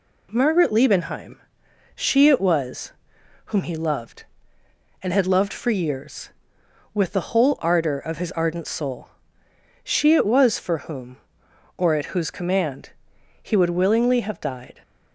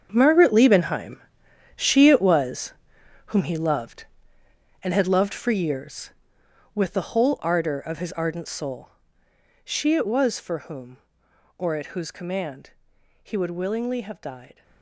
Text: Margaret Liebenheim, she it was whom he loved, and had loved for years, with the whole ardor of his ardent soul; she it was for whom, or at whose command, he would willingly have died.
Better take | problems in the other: first | gets quieter; strong; throughout; 13.5 dB // pauses between "was" and "whom"; noticeable; at 2.7 s; 0.54 s long; noticeable in the first

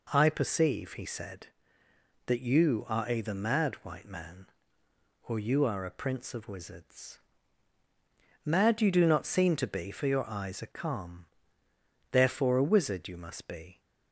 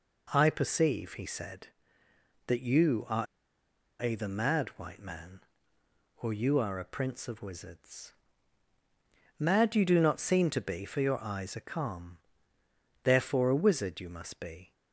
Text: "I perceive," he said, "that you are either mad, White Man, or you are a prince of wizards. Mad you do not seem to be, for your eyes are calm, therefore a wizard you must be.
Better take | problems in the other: first | pauses between "are" and "either"; noticeable; at 3.2 s; 0.78 s long

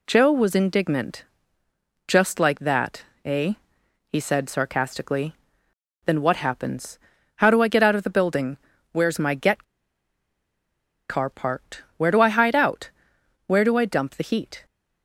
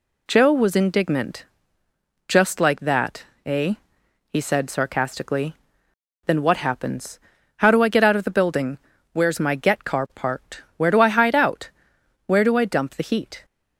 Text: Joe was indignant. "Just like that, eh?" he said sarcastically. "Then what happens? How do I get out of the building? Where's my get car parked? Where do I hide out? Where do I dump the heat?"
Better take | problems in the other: second | pauses between "get" and "car"; strong; at 9.6 s; 1.4 s long

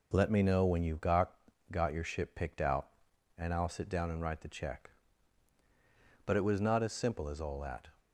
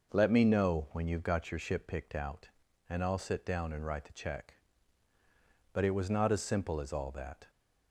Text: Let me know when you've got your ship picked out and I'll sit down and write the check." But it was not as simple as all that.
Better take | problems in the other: second | says "got" twice; at 1.7 s

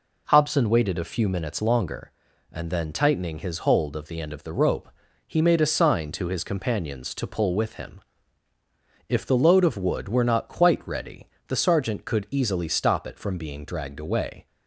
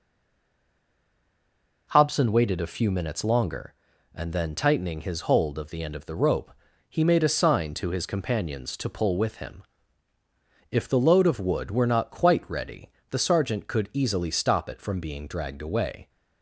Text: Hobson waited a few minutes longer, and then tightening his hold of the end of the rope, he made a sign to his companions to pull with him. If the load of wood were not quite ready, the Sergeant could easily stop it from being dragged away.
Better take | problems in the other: first | stays silent before the first word; noticeable; until 1.8 s; 1.8 s long

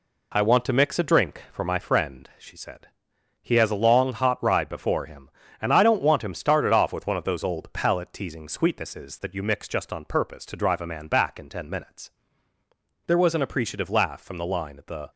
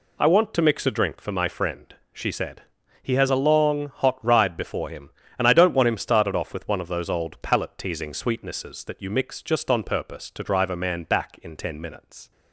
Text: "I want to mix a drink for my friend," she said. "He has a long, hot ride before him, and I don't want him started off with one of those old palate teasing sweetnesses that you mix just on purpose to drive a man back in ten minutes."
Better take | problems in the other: second | goes on to say "There was an appreciative laugh from the line at the"; strong; from 13.0 s on; 2.0 s long

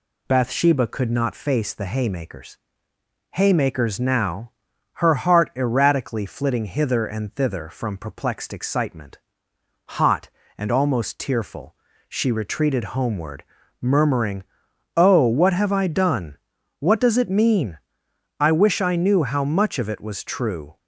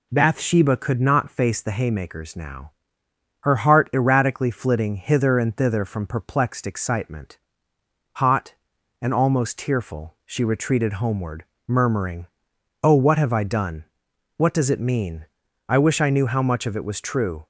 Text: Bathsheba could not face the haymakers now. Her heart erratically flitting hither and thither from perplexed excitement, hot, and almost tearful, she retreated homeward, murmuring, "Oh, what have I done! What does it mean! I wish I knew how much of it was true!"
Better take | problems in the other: second | says "haymakers" twice; at 3.3 s

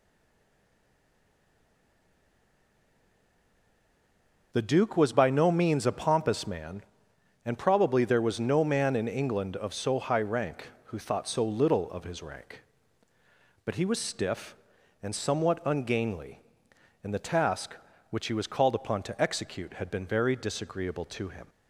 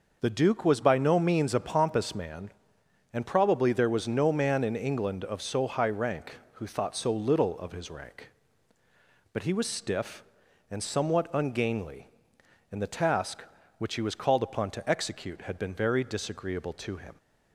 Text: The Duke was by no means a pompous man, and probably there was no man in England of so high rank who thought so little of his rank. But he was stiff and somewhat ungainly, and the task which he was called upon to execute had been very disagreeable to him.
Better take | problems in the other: second | stays silent before the first word; strong; until 4.5 s; 4.5 s long

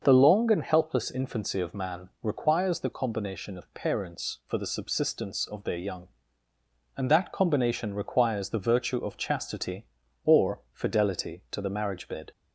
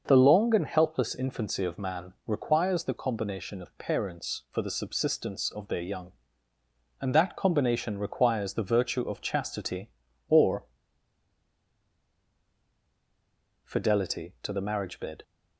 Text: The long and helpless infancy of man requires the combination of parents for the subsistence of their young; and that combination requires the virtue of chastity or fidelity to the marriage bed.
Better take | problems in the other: first | starts louder than the rest; until 1.0 s; 6 dB; also in the first // pauses between "man" and "requires"; slight; at 2.1 s; 0.16 s long; slight in the first // pauses between "or" and "fidelity"; strong; at 10.6 s; 2.9 s long

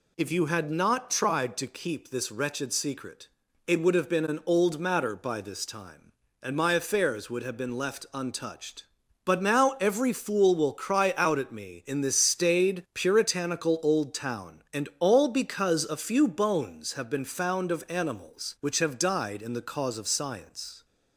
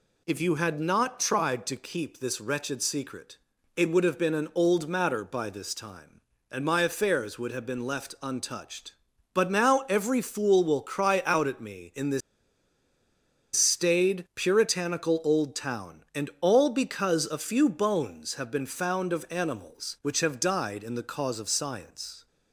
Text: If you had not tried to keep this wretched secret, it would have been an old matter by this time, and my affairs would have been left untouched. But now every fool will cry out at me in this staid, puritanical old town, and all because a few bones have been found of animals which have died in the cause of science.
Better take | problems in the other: first | pauses between "this" and "staid"; strong; at 12.2 s; 1.3 s long

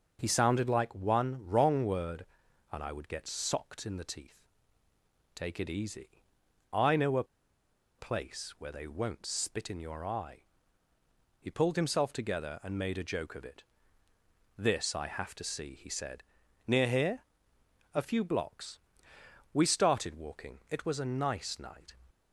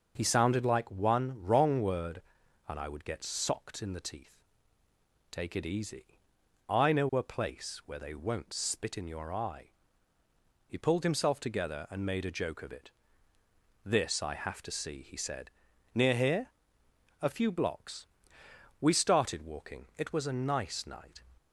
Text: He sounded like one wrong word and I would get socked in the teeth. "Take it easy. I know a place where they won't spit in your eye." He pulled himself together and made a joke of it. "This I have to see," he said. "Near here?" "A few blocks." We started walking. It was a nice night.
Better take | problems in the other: second | starts louder than the rest; noticeable; until 1.2 s; 6 dB; also in the second // pauses between "a" and "place"; noticeable; at 7.2 s; 0.74 s long

